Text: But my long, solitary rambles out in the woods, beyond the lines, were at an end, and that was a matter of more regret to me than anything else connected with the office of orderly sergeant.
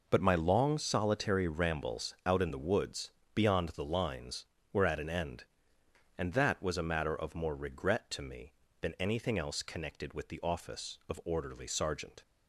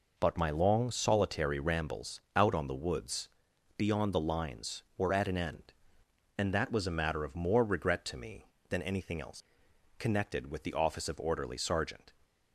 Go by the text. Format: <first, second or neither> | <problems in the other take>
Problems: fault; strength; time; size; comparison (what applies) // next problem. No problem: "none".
first | says "on" for "in"; at 2.5 s // pauses between "else" and "connected"; noticeable; at 9.4 s; 0.54 s long